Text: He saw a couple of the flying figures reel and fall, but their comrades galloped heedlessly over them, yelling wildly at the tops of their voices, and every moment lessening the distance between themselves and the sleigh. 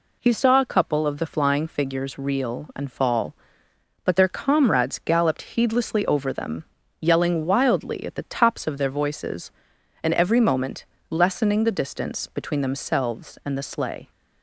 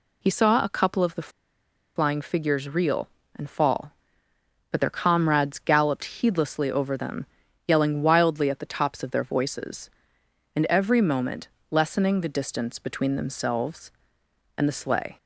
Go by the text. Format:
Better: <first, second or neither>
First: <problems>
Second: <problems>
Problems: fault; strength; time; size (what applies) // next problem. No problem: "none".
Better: first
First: pauses between "moment" and "lessening"; slight; at 10.8 s; 0.26 s long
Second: pauses between "the" and "flying"; noticeable; at 1.2 s; 0.67 s long // pauses between "moment" and "lessening"; slight; at 11.4 s; 0.22 s long